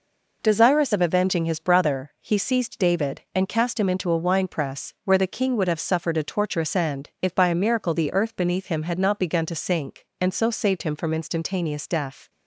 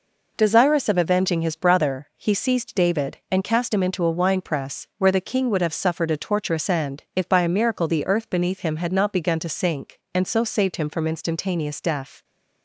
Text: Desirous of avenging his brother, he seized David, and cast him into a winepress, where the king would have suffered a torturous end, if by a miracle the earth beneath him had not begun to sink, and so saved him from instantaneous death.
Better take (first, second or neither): neither